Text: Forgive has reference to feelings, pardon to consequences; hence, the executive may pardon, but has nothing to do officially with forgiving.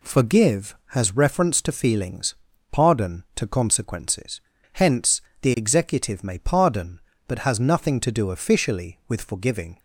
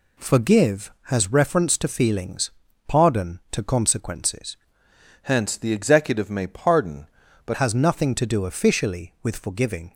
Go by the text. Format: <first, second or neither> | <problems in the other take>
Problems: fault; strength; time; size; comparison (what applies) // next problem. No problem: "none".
first | changes voice from "hence" to "but"; from 5.2 to 7.5 s; 2.3 s long